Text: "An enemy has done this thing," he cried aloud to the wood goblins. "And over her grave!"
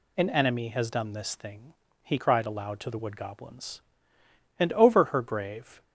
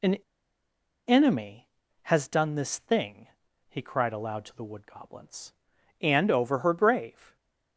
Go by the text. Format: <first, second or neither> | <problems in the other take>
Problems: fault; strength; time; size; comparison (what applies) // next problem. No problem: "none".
first | pauses between "An" and "enemy"; noticeable; at 0.1 s; 0.93 s long